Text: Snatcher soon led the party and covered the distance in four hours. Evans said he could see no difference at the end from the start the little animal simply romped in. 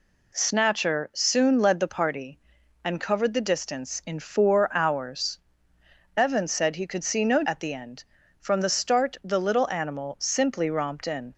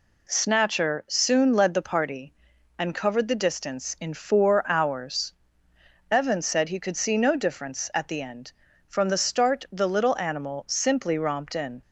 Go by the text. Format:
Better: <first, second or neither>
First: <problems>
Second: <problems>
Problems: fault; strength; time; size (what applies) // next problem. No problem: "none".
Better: second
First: skips "difference"; at 7.4 s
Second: none